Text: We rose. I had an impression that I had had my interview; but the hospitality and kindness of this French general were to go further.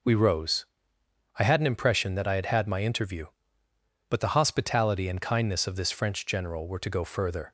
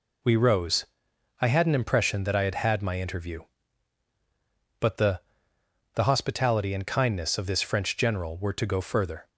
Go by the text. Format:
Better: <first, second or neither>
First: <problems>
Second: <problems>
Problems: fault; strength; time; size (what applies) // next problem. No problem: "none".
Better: first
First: none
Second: says "the" twice; at 5.9 s